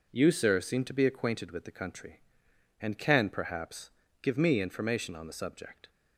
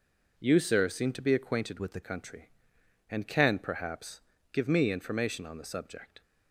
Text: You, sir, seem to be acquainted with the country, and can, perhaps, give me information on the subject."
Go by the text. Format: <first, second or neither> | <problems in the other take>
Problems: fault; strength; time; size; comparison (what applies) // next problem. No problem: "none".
first | changes voice from "with" to "the"; from 1.7 to 2.0 s; 0.3 s long